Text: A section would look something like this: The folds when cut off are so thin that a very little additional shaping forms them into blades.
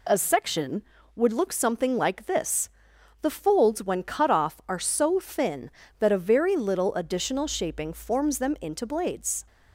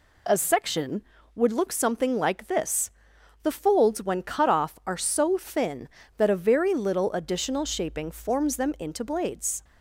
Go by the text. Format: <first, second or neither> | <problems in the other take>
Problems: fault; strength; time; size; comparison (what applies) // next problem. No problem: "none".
neither | none